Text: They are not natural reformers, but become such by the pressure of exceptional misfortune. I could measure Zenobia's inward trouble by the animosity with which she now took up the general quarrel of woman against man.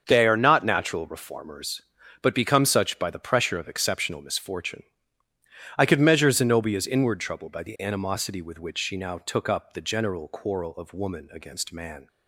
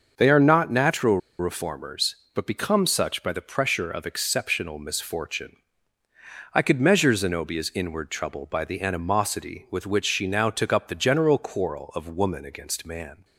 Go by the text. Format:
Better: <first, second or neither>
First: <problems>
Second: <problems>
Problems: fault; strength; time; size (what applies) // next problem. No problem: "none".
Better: first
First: starts louder than the rest; until 1.0 s; 6.5 dB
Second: starts louder than the rest; until 1.1 s; 6 dB // pauses between "natural" and "reformers"; slight; at 1.1 s; 0.22 s long